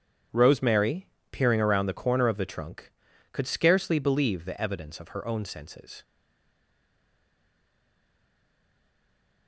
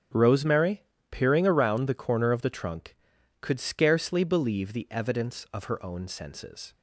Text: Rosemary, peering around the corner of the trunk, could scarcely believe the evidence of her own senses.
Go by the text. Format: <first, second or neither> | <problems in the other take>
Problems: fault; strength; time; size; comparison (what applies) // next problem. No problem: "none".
second | starts louder than the rest; strong; until 1.5 s; 9 dB; strong in the second // stays silent after the last word; strong; from 6.0 s on; 3.4 s long